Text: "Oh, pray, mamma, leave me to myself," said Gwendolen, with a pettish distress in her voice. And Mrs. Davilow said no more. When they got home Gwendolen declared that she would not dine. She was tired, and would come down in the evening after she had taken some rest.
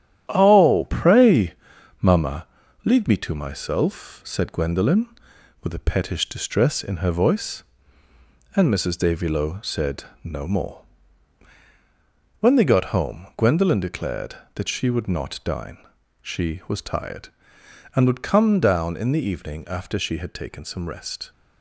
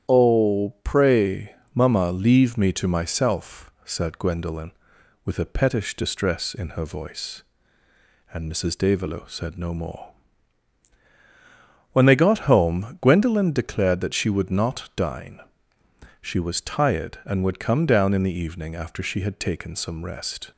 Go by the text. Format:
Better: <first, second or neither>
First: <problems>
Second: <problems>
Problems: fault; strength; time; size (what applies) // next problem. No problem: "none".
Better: second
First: gets quieter; throughout; 6.5 dB // starts louder than the rest; strong; until 1.3 s; 10.5 dB // pauses between "said" and "no"; slight; at 10.0 s; 0.22 s long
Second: starts louder than the rest; strong; until 1.1 s; 10 dB